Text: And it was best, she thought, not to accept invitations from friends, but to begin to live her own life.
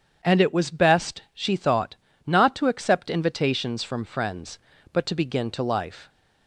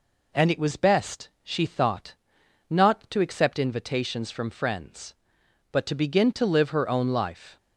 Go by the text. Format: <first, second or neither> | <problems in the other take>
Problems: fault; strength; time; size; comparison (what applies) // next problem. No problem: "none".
second | starts louder than the rest; strong; until 1.3 s; 7.5 dB // skips "live her own"; at 5.6 s